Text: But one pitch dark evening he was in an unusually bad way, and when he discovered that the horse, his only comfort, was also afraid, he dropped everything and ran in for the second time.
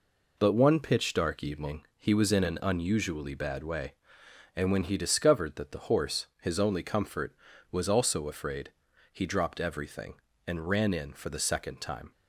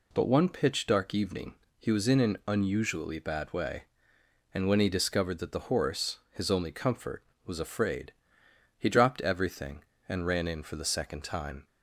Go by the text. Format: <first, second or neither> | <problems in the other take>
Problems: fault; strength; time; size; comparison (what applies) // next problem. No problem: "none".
first | pauses between "evening" and "he"; slight; at 1.5 s; 0.24 s long // skips "also"; at 7.5 s